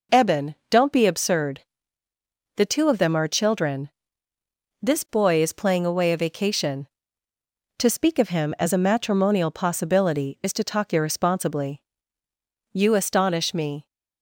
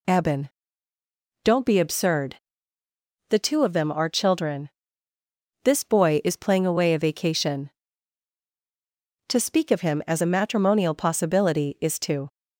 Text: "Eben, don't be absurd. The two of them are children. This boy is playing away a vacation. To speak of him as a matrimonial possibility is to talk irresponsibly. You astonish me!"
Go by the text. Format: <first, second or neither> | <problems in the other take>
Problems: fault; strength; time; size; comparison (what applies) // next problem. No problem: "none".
first | stops before "talk irresponsibly You astonish me"; at 12.3 s